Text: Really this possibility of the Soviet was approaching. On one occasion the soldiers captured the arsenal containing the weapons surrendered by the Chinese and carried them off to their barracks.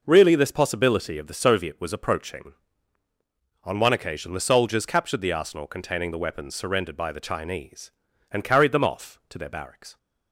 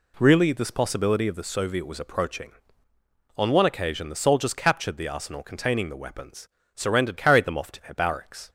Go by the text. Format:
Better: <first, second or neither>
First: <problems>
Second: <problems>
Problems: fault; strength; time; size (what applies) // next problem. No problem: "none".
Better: first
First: none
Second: pauses between "weapons" and "surrendered"; slight; at 6.4 s; 0.30 s long // skips "by the Chinese and"; at 7.1 s